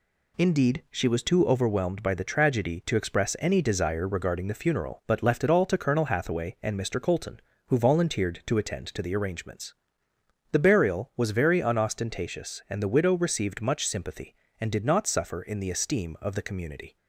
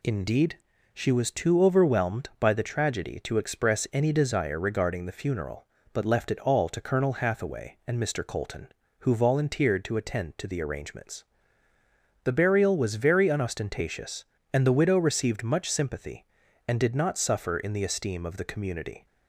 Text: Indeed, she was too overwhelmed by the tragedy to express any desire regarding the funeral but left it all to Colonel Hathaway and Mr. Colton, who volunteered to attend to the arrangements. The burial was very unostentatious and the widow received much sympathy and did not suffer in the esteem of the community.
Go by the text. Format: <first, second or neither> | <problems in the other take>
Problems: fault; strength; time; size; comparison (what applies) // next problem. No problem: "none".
neither | none